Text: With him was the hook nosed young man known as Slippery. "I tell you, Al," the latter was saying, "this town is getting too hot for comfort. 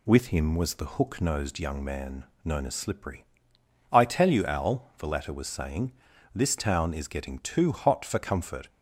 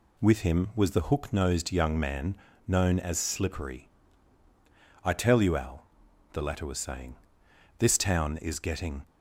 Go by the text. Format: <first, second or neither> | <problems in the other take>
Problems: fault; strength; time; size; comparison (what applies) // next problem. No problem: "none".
first | pauses between "man" and "known"; slight; at 2.3 s; 0.32 s long; slight in the first // stops before "too hot for comfort"; at 9.0 s